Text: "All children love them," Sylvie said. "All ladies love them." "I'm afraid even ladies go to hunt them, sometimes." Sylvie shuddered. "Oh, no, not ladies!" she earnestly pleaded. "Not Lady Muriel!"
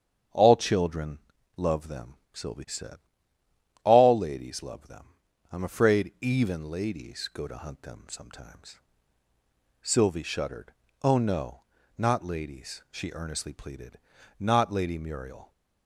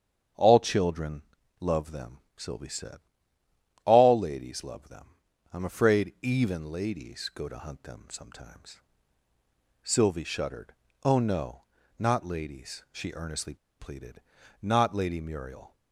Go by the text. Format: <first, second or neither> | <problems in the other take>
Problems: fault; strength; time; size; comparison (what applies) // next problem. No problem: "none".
first | starts louder than the rest; strong; until 1.7 s; 8 dB; strong in the first // pauses between "children" and "love"; slight; at 1.2 s; 0.36 s long; slight in the first // pauses between "earnestly" and "pleaded"; slight; at 13.5 s; 0.24 s long